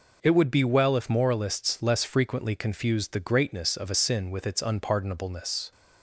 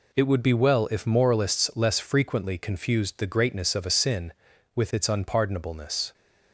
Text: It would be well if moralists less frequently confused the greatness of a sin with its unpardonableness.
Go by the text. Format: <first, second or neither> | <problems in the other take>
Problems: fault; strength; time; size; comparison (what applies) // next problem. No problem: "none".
neither | none